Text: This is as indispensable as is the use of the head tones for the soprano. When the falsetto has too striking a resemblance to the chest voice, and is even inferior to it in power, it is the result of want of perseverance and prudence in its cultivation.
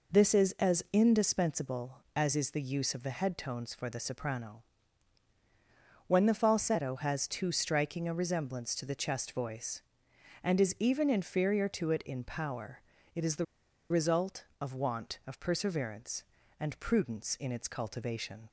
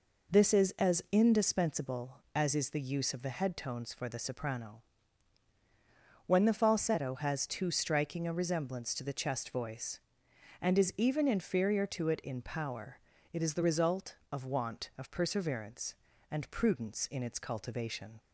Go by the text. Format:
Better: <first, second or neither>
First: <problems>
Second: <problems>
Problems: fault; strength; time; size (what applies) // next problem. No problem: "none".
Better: second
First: pauses between "the" and "result"; at 13.4 s; 0.45 s long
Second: none